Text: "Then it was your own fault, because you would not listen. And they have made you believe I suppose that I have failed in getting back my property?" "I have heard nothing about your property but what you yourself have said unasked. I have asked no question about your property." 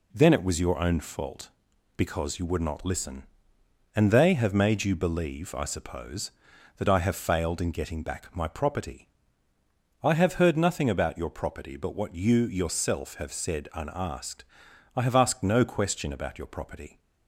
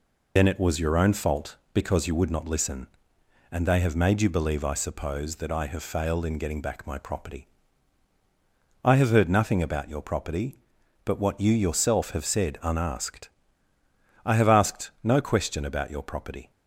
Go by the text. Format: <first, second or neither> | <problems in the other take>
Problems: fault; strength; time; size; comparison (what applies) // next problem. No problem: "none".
first | loses the start of "Then"; at 0.3 s; 70 ms